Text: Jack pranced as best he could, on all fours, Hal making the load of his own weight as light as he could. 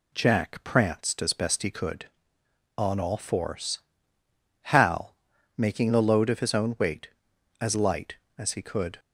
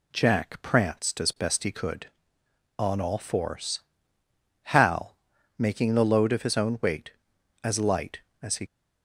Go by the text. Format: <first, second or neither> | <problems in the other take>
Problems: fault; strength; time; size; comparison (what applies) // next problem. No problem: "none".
first | pauses between "Hal" and "making"; at 5.1 s; 0.42 s long; also in the first // stops before "could"; at 8.6 s